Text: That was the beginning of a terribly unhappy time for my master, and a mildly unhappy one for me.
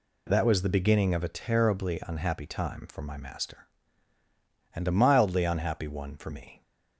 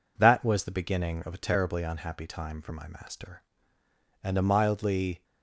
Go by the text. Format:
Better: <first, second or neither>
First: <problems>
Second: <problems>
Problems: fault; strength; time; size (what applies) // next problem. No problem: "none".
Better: first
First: none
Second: stops before "unhappy one for me"; at 5.2 s